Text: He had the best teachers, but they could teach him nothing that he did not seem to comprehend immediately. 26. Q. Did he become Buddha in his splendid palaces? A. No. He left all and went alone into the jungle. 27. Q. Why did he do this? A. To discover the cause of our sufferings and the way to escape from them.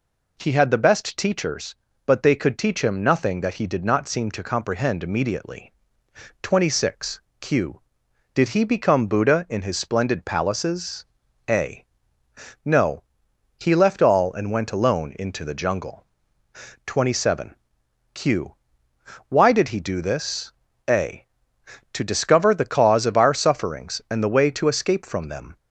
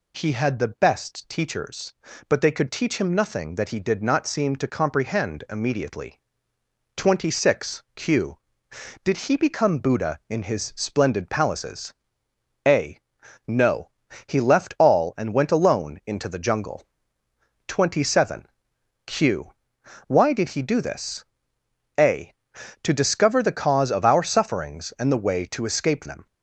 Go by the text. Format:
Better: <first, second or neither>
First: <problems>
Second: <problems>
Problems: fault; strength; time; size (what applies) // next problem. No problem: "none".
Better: first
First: none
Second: skips "from"; at 26.0 s